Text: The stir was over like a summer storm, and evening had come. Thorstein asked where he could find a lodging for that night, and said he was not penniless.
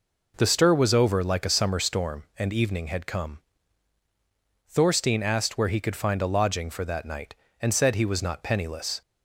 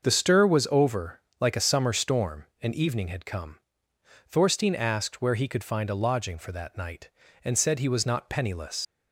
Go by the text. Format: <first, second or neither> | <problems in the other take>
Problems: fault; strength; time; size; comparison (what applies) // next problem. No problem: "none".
first | starts louder than the rest; until 1.0 s; 6.5 dB // pauses between "over" and "like"; slight; at 1.2 s; 0.18 s long // leaves "penniless" unfinished; at 8.8 s; 105 ms